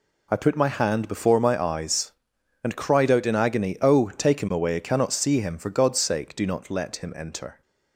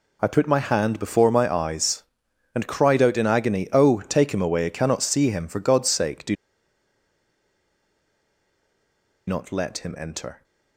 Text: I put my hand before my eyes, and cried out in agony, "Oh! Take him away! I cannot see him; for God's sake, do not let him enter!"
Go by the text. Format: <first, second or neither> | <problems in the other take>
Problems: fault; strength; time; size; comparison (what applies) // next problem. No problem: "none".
first | pauses between "do" and "not"; strong; at 6.3 s; 2.9 s long